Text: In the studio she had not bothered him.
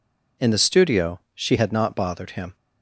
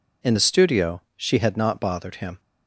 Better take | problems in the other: neither | pauses between "studio" and "she"; slight; the same in both

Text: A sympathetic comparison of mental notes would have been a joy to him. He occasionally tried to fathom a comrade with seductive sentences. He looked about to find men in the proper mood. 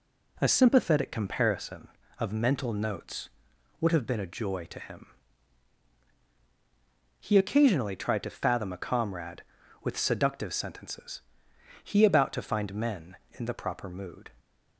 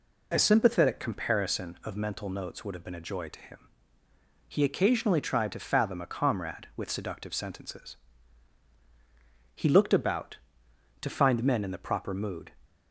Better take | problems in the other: second | skips "looked"; at 12.0 s

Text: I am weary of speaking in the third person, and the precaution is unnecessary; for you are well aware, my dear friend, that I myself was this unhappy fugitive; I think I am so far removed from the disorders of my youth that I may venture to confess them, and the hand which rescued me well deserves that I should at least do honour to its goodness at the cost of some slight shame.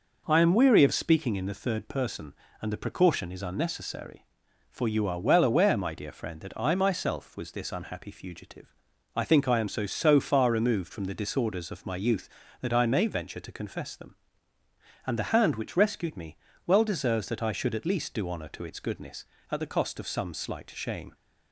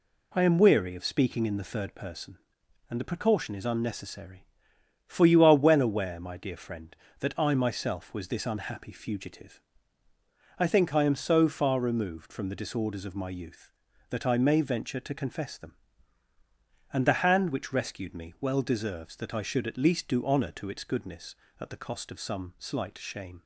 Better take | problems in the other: second | says "so" twice; at 9.8 s // pauses between "me" and "well"; slight; at 16.3 s; 0.26 s long

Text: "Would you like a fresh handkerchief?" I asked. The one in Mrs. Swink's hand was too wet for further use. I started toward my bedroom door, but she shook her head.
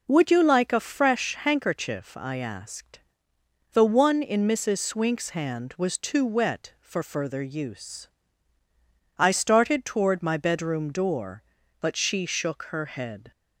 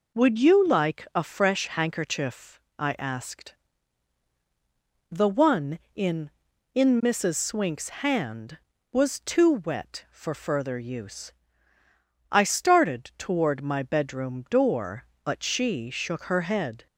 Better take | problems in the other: first | says "in" twice; at 6.7 s

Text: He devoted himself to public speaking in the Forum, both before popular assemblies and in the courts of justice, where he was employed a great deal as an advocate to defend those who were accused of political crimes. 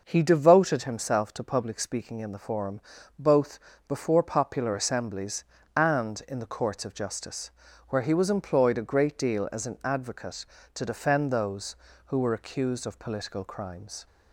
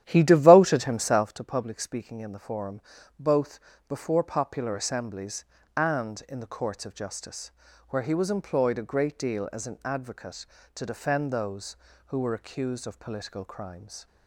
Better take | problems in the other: first | starts louder than the rest; strong; until 1.4 s; 11.5 dB // pauses between "both" and "before"; slight; at 3.5 s; 0.30 s long; slight in the first

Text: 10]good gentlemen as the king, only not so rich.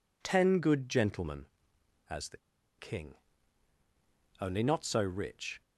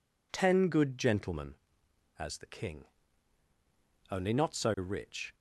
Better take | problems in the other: second | pauses between "the" and "king"; at 2.3 s; 0.41 s long

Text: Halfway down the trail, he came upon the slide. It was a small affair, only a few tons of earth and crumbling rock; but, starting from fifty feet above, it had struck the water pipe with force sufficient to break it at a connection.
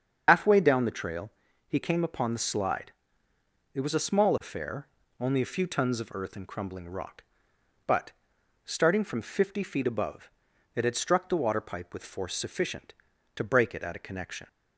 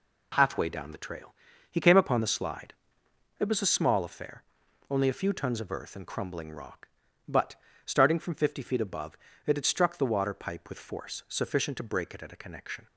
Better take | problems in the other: second | loses the start of "Halfway"; at 0.2 s; 70 ms // starts louder than the rest; until 1.2 s; 6.5 dB

